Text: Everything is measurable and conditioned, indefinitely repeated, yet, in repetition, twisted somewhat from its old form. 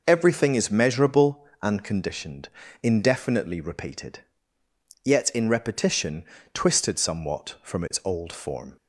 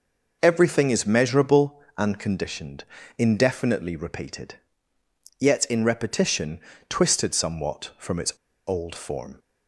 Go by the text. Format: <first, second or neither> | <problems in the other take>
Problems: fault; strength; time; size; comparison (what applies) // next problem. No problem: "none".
first | starts louder than the rest; noticeable; until 1.4 s; 6 dB; noticeable in the first // pauses between "its" and "old"; slight; at 8.3 s; 0.36 s long